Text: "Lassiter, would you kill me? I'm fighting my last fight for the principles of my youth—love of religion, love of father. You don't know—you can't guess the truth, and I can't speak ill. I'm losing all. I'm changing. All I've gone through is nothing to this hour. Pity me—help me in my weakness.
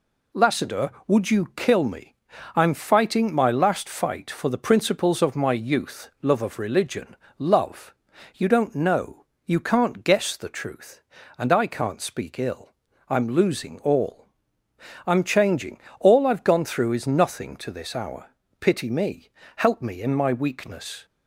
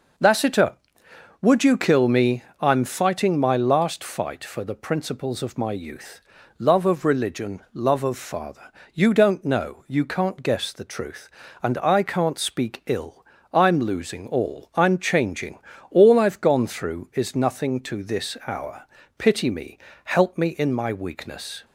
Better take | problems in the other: second | skips "of father"; at 8.1 s

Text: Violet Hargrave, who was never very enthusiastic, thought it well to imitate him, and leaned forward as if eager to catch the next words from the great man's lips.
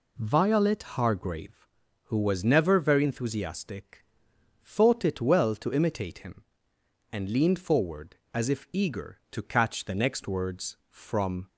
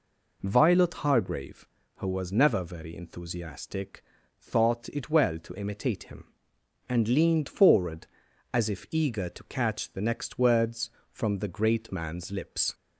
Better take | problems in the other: second | stops before "the great man's lips"; at 11.4 s

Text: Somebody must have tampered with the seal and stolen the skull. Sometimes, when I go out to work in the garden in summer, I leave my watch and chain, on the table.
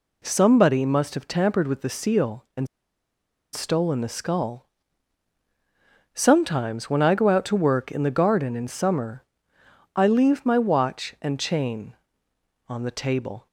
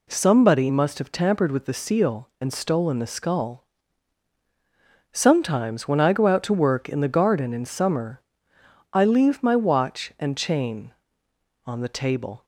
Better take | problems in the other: second | pauses between "and" and "stolen"; noticeable; at 2.6 s; 0.87 s long

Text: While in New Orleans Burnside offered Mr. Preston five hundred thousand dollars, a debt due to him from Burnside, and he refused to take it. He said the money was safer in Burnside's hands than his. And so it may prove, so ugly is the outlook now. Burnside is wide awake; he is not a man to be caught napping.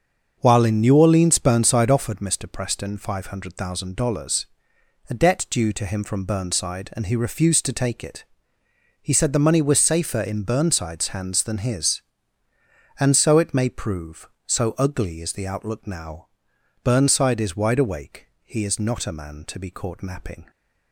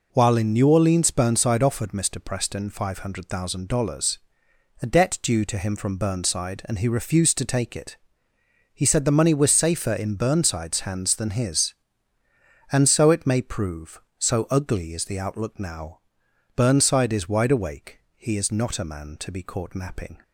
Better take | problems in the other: second | starts louder than the rest; until 2.2 s; 6.5 dB

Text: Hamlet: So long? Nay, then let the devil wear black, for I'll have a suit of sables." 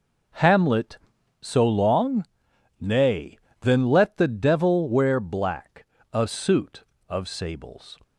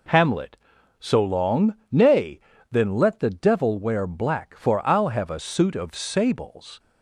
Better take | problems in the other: second | skips "for I'll have"; at 5.9 s

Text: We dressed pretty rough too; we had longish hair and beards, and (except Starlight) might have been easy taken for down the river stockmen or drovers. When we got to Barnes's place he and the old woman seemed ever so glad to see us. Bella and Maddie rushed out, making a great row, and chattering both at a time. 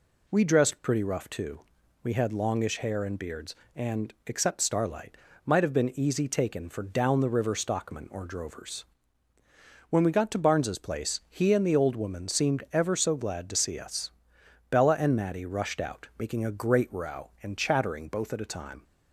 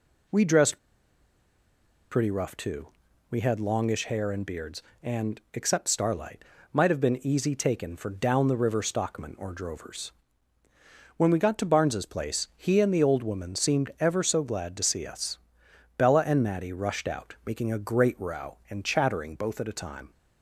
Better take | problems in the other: first | pauses between "dressed" and "pretty"; strong; at 0.7 s; 1.3 s long

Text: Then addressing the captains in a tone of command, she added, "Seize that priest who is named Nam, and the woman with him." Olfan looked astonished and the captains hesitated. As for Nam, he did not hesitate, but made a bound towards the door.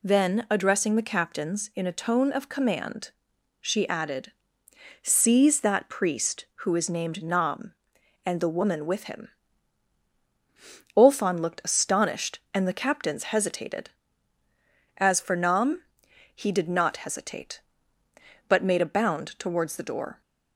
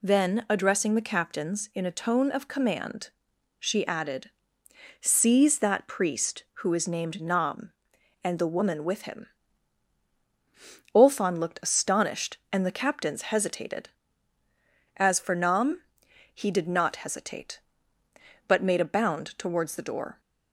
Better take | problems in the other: neither | none

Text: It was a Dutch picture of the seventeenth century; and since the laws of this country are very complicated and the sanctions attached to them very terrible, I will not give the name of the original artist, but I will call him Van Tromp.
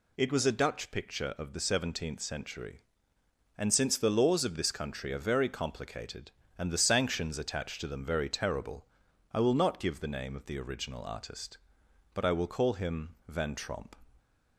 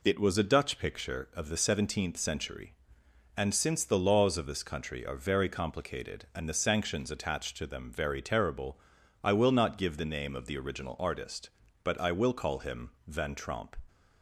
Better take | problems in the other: neither | none

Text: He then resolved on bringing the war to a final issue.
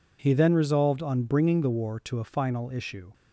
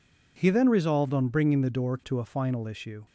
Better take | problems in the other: first | says "door" for "war"; at 1.7 s

